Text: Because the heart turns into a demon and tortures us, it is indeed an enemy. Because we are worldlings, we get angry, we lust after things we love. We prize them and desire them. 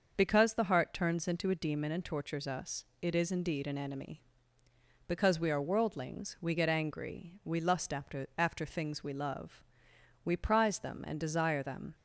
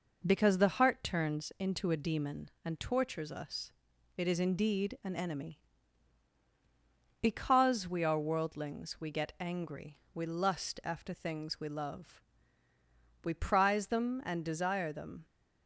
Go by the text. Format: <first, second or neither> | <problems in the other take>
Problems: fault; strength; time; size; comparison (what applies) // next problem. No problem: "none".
second | starts louder than the rest; noticeable; until 1.1 s; 6 dB // says "after" twice; at 8.3 s